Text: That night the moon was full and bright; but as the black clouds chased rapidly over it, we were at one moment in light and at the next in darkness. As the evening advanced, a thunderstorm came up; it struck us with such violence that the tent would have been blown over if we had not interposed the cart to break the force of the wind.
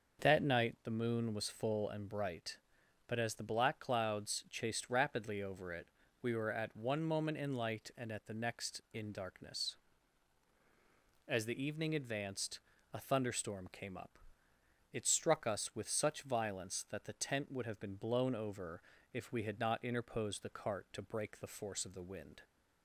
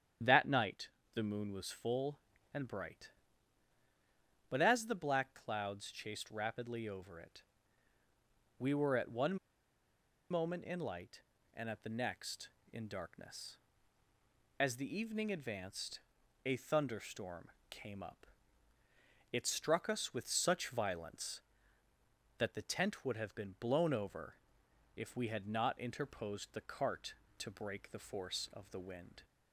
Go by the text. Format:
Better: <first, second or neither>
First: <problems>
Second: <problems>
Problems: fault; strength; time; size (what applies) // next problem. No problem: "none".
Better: first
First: starts louder than the rest; noticeable; until 1.2 s; 6 dB // pauses between "over" and "if"; slight; at 18.8 s; 0.32 s long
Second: starts louder than the rest; strong; until 1.5 s; 9.5 dB // pauses between "night" and "the"; slight; at 0.8 s; 0.28 s long // pauses between "one" and "moment"; noticeable; at 9.3 s; 0.94 s long // pauses between "thunderstorm" and "came"; slight; at 17.4 s; 0.20 s long // pauses between "over" and "if"; noticeable; at 24.3 s; 0.62 s long